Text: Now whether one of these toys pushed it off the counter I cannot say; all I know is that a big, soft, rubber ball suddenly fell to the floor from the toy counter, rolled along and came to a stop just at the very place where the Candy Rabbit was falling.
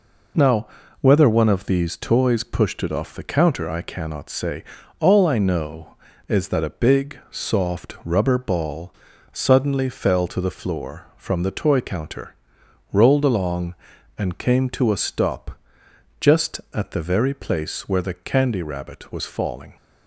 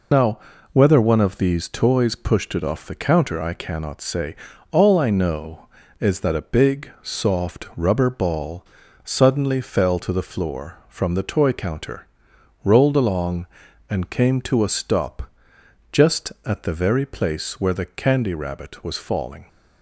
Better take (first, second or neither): first